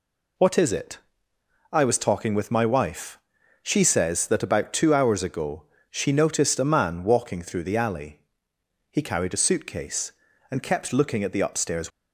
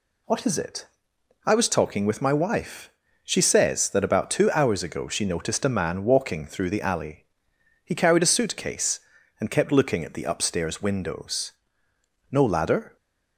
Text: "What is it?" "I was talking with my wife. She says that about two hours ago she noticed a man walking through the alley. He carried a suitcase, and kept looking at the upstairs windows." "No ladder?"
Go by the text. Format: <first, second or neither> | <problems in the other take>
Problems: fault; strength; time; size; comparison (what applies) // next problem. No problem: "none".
second | pauses between "ago" and "she"; slight; at 5.6 s; 0.30 s long // stops before "windows No ladder"; at 11.9 s